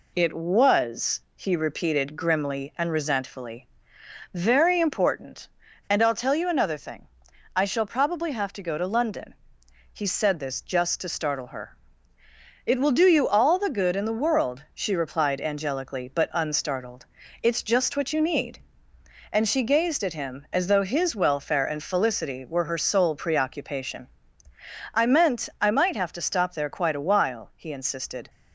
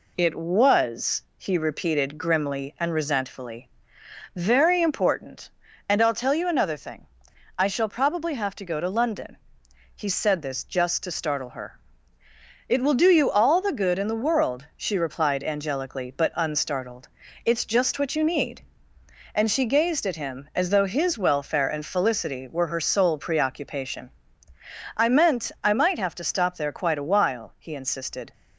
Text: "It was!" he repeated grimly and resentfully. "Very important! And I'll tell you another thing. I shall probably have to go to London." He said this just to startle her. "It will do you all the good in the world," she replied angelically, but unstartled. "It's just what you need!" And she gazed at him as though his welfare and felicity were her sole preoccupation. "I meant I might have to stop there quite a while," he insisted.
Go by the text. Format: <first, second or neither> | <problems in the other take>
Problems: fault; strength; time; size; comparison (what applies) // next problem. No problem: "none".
neither | none